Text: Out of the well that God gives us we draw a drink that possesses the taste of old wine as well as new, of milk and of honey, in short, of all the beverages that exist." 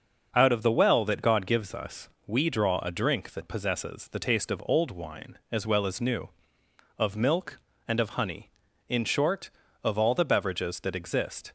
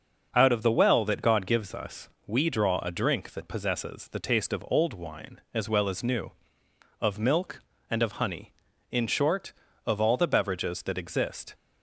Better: neither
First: pauses between "us" and "we"; slight; at 2.0 s; 0.18 s long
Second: pauses between "us" and "we"; slight; at 2.0 s; 0.18 s long

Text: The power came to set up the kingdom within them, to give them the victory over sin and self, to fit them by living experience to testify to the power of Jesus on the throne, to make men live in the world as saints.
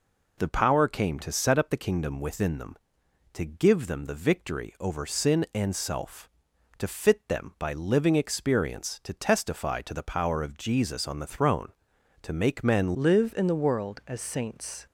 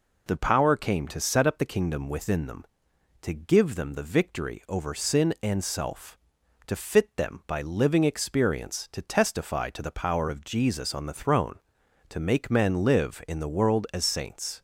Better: second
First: changes voice at "live"; from 12.9 s on; 1.9 s long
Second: none

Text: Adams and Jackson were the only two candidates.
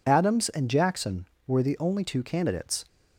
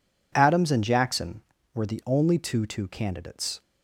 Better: first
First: none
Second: says "two" twice; at 2.6 s

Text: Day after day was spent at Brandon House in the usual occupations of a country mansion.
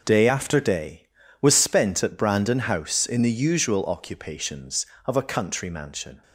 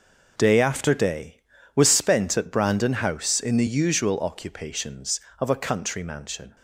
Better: neither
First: none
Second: none

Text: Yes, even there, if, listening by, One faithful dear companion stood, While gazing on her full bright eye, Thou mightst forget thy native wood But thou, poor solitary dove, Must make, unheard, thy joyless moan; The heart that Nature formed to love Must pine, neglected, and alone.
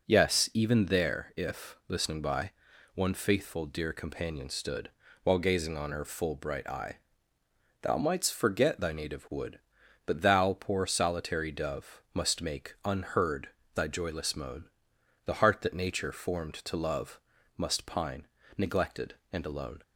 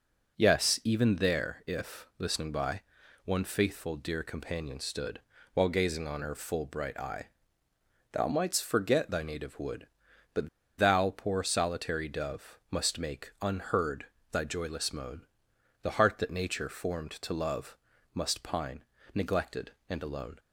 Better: first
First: pauses between "love" and "Must"; slight; at 17.1 s; 0.36 s long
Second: pauses between "But" and "thou"; slight; at 10.4 s; 0.30 s long // pauses between "love" and "Must"; slight; at 17.7 s; 0.36 s long

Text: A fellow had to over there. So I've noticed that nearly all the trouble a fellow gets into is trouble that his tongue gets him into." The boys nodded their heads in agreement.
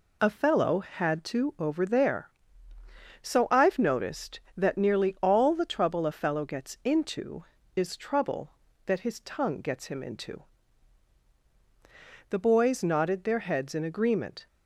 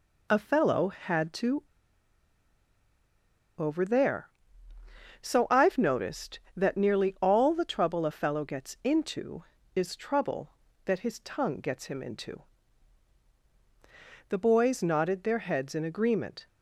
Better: first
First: none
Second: pauses between "to" and "over"; strong; at 1.6 s; 1.9 s long

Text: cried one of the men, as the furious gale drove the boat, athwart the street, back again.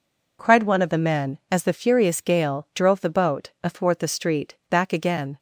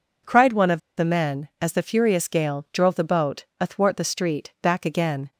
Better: first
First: none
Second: pauses between "of" and "the"; slight; at 0.8 s; 0.17 s long

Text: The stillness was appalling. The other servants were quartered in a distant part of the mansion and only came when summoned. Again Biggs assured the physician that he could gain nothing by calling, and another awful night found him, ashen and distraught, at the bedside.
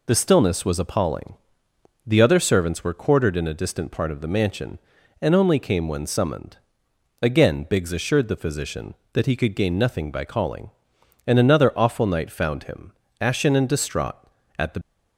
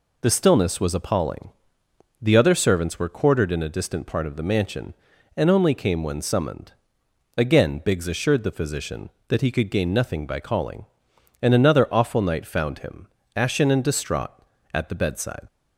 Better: second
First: stops before "bedside"; at 14.8 s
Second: none

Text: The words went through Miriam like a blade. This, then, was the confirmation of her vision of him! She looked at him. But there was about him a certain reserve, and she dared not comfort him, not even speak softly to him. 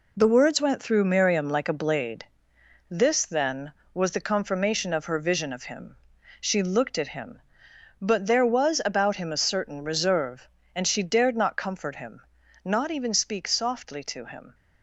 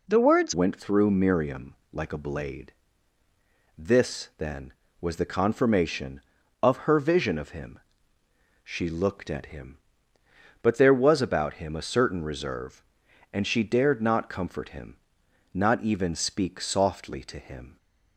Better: first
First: none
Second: changes voice at "went"; from 0.5 s on; 17.2 s long // pauses between "Miriam" and "like"; slight; at 1.7 s; 0.18 s long

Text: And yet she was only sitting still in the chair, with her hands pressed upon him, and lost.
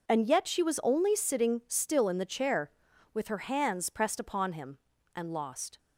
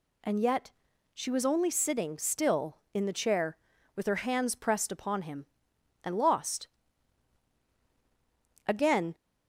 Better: first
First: none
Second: pauses between "yet" and "she"; at 0.7 s; 0.42 s long // goes on to say "Again"; slight; from 8.6 s on; 0.48 s long

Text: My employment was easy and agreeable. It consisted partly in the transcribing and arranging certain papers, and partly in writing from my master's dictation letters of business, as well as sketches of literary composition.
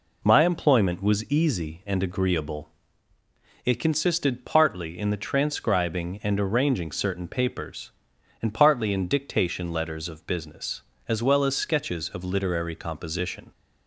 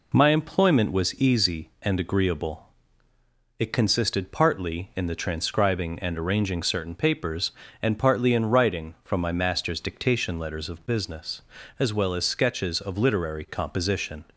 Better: second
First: skips "writing from my master's"; at 9.0 s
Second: none

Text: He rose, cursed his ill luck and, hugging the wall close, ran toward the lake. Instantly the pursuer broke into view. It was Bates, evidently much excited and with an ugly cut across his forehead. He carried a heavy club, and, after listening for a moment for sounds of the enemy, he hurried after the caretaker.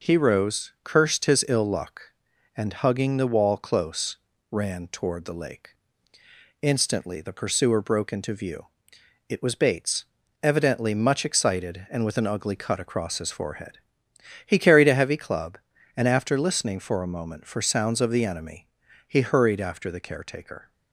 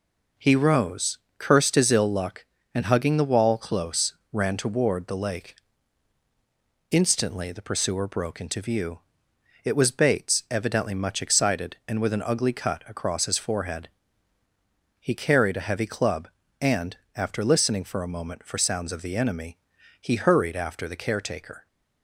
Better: neither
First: none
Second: none

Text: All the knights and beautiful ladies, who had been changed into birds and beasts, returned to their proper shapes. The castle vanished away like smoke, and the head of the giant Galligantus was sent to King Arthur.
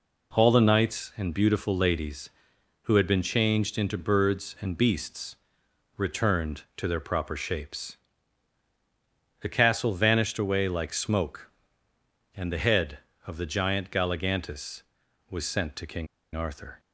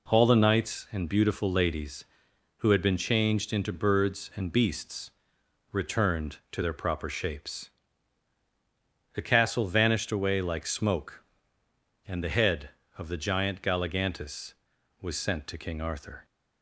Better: second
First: pauses between "King" and "Arthur"; slight; at 16.0 s; 0.27 s long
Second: none

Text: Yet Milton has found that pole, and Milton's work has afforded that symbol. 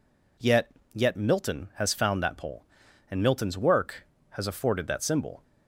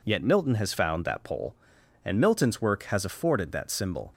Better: second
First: says "Yet" twice; at 0.9 s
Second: none

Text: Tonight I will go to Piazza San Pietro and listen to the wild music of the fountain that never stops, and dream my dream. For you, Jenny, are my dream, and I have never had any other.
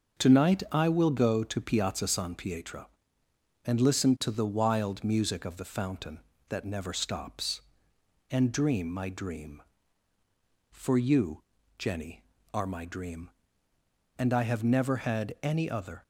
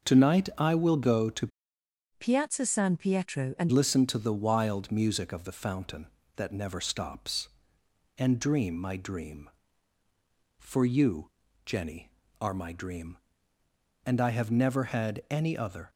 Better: first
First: starts louder than the rest; until 1.2 s; 6.5 dB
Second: starts louder than the rest; until 1.1 s; 6.5 dB // changes voice from "Piazza" to "and"; from 2.1 to 3.7 s; 1.6 s long

